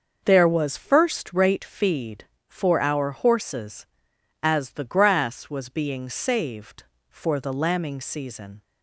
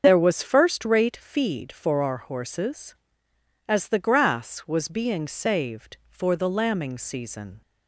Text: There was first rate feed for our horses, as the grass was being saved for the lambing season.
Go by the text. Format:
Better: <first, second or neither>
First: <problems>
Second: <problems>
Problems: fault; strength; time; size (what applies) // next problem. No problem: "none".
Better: first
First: starts louder than the rest; until 1.2 s; 6.5 dB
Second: loses the start of "There"; at 0.0 s; 40 ms // starts louder than the rest; until 1.0 s; 7 dB